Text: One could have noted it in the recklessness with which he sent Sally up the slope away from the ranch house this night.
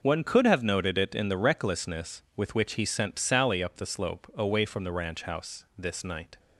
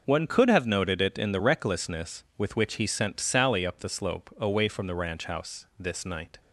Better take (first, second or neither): neither